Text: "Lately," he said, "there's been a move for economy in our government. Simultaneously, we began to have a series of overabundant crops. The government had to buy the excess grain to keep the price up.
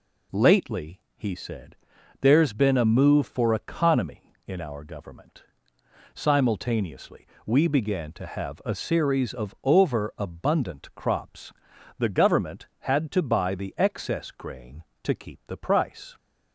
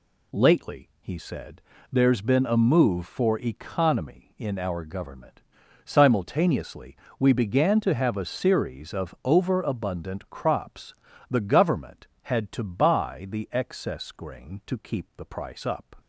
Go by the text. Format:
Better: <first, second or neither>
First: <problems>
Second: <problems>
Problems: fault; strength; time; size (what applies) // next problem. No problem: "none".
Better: second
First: stops before "up"; at 16.1 s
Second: none